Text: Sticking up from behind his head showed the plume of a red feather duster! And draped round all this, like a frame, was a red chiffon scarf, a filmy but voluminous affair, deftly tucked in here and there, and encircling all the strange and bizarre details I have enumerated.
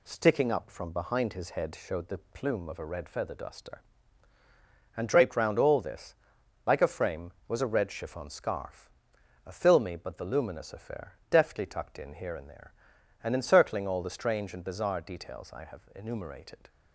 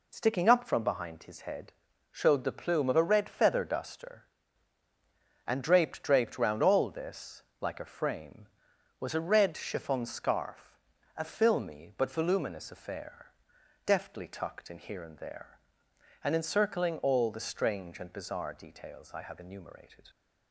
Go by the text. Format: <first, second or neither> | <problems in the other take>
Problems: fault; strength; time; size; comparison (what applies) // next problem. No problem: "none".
first | pauses between "head" and "showed"; at 1.7 s; 0.40 s long // says "draped" twice; at 6.0 s